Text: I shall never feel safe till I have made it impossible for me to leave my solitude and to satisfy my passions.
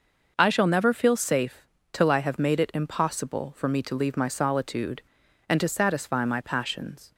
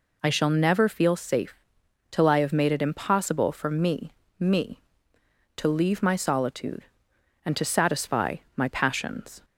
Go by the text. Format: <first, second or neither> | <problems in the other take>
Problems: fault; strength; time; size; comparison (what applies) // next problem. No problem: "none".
first | pauses between "safe" and "till"; noticeable; at 1.5 s; 0.56 s long; slight in the first // says "me" twice; at 4.4 s // pauses between "satisfy" and "my"; slight; at 8.3 s; 0.18 s long